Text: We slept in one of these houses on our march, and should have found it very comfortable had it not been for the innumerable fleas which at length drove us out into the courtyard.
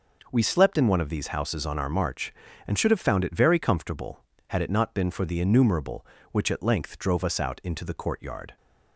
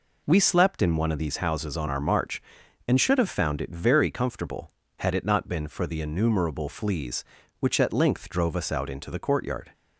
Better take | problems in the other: second | skips "fleas"; at 6.1 s

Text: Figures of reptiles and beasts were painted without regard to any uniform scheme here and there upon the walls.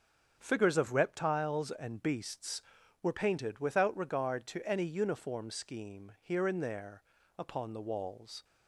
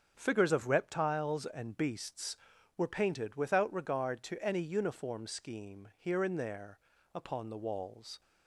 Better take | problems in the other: neither | starts louder than the rest; the same in both // pauses between "there" and "upon"; slight; the same in both

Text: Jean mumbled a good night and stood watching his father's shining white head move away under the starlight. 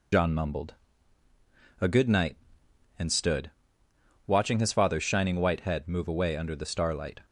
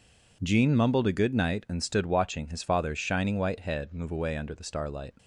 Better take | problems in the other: second | loses the start of "Jean"; at 0.1 s; 75 ms // pauses between "mumbled" and "a"; at 0.7 s; 1.0 s long // pauses between "stood" and "watching"; noticeable; at 3.4 s; 0.76 s long

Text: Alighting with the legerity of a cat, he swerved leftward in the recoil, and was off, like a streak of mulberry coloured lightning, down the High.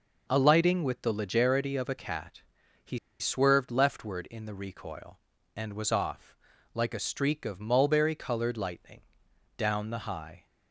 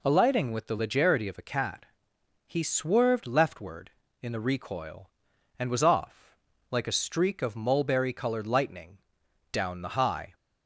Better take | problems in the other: second | pauses between "he" and "swerved"; slight; at 2.9 s; 0.21 s long

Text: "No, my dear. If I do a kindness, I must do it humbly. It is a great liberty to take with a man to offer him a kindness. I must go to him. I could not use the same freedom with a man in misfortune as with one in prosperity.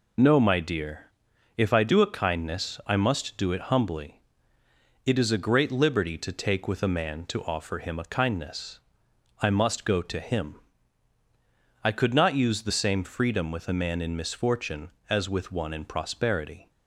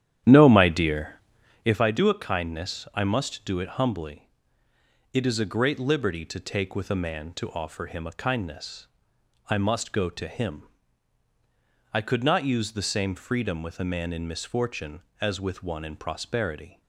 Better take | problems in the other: first | starts louder than the rest; strong; until 1.8 s; 10.5 dB

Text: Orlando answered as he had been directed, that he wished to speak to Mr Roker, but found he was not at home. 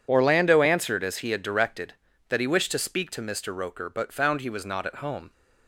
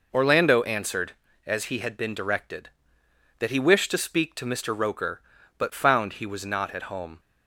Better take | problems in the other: second | skips "been"; at 1.4 s

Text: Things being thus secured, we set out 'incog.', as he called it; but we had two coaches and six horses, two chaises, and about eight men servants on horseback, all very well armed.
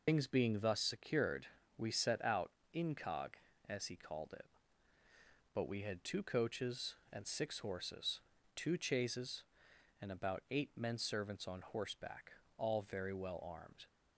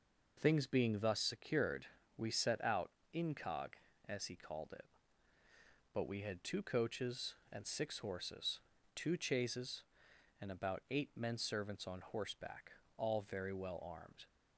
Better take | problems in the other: second | loses the start of "Things"; at 0.0 s; 100 ms // pauses between "out" and "incog"; slight; at 2.5 s; 0.22 s long; slight in the second

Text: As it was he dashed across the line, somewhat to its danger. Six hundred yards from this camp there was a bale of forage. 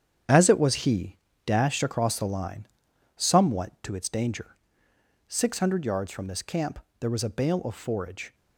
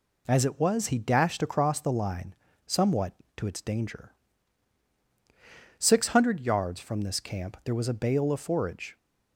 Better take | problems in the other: second | gets quieter; strong; throughout; 9 dB // pauses between "he" and "dashed"; slight; at 1.1 s; 0.28 s long // pauses between "camp" and "there"; slight; at 6.7 s; 0.22 s long

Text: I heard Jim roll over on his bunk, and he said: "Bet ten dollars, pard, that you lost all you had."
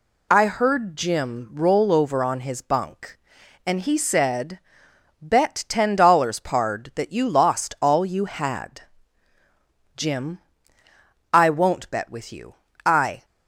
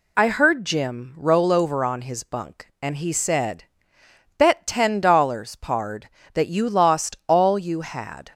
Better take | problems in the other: second | goes on to say "Jim I won't bet with you I"; strong; from 9.9 s on; 3.2 s long

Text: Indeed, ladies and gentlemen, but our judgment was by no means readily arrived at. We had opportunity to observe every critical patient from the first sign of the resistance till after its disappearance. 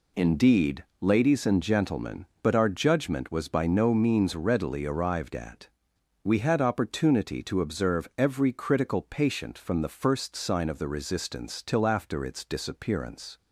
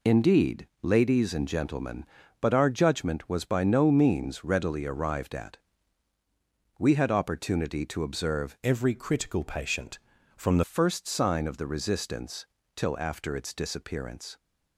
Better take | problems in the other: first | changes voice from "every" to "the"; from 8.6 to 10.6 s; 2.0 s long // pauses between "resistance" and "till"; slight; at 12.4 s; 0.30 s long

